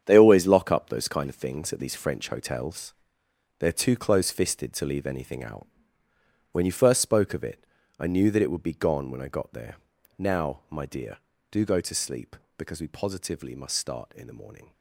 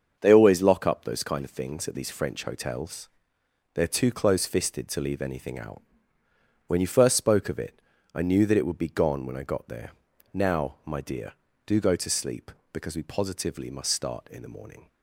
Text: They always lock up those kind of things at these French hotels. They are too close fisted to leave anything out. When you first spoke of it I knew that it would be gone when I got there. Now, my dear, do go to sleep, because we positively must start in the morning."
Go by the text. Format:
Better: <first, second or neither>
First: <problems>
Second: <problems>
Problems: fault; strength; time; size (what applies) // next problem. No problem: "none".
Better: second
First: gets quieter; strong; throughout; 11.5 dB // starts louder than the rest; strong; until 1.0 s; 8.5 dB // pauses between "it" and "I"; slight; at 7.6 s; 0.34 s long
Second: starts louder than the rest; until 1.2 s; 6.5 dB // pauses between "it" and "I"; slight; at 7.7 s; 0.34 s long